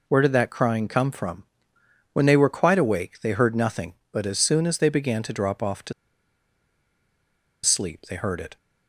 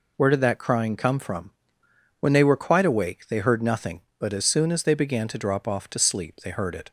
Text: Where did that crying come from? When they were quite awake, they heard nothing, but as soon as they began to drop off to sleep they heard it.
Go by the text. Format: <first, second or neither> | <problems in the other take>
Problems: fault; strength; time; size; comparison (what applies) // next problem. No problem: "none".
second | pauses between "to" and "sleep"; strong; at 5.9 s; 1.7 s long